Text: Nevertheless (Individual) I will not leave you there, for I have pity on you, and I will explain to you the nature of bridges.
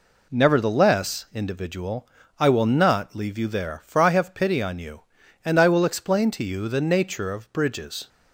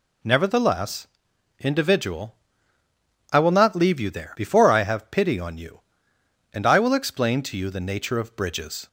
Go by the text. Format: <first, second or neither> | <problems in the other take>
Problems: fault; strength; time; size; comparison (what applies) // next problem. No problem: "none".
first | says "before" for "for"; at 4.3 s